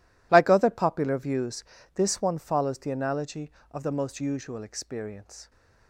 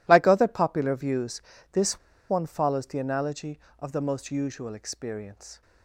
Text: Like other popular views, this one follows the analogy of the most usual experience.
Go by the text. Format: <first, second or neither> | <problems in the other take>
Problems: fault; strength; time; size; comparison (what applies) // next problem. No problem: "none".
first | pauses between "this" and "one"; slight; at 1.9 s; 0.32 s long